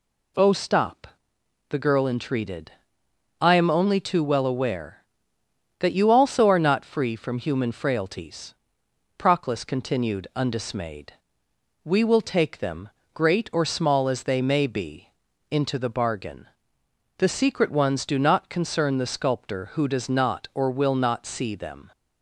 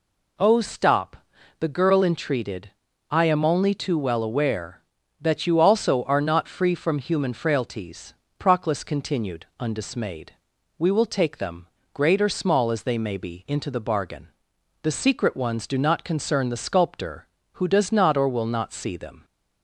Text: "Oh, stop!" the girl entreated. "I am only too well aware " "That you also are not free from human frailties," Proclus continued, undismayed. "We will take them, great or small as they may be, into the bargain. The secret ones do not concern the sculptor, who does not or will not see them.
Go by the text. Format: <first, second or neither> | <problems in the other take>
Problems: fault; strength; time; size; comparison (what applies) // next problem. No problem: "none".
neither | none